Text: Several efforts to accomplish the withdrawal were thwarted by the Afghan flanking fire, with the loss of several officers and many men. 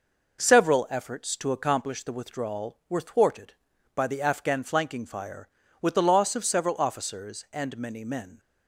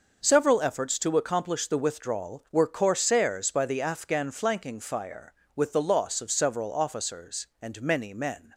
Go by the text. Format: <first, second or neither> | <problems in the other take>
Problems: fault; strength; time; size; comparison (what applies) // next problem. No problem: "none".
first | says "corsairs" for "thwarted"; at 2.6 s